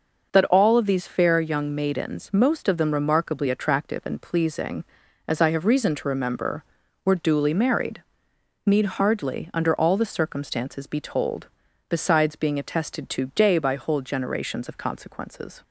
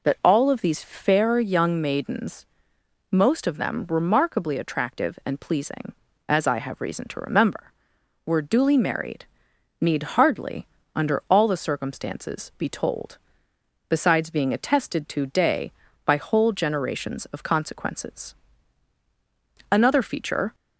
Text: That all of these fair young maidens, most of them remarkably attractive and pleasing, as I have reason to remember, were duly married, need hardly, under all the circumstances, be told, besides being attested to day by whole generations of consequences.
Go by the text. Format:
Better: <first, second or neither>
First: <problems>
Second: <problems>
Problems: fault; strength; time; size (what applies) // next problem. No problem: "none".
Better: first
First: none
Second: goes on to say "Another feature"; noticeable; from 19.7 s on; 0.84 s long